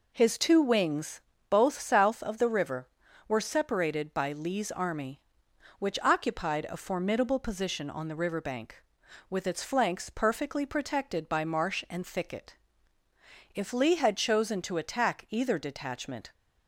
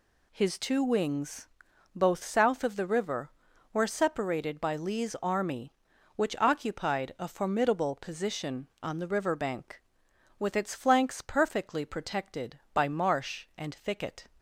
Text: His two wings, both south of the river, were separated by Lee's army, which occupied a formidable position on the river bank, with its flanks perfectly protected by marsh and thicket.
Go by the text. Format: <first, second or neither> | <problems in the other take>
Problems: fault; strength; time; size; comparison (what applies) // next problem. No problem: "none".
second | goes on to say "If Lee had chosen to attack either detachment"; strong; from 13.5 s on; 2.7 s long